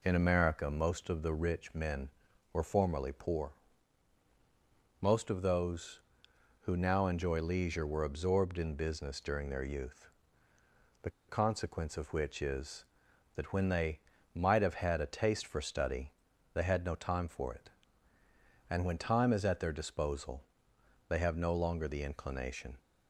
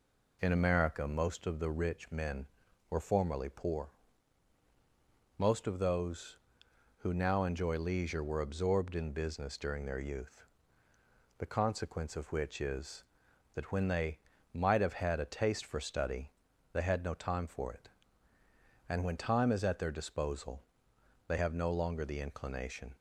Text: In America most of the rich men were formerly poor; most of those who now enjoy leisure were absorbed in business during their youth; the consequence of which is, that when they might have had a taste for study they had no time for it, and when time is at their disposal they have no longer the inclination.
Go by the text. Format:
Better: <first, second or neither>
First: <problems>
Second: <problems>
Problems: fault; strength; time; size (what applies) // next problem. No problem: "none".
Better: second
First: pauses between "the" and "consequence"; slight; at 11.1 s; 0.17 s long // pauses between "they" and "might"; slight; at 13.9 s; 0.34 s long // pauses between "study" and "they"; at 16.1 s; 0.40 s long // pauses between "disposal" and "they"; noticeable; at 20.4 s; 0.64 s long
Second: pauses between "they" and "might"; slight; at 14.1 s; 0.34 s long // pauses between "study" and "they"; at 16.3 s; 0.40 s long // pauses between "disposal" and "they"; noticeable; at 20.6 s; 0.64 s long